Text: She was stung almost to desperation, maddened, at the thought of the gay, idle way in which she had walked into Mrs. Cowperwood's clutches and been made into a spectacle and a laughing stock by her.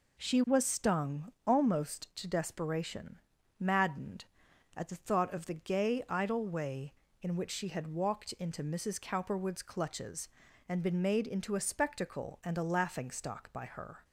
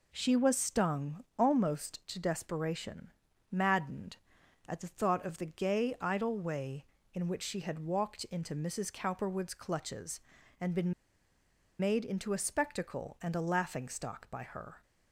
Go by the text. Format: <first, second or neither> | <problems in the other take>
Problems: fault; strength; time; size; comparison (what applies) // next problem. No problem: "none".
first | pauses between "been" and "made"; noticeable; at 10.9 s; 0.87 s long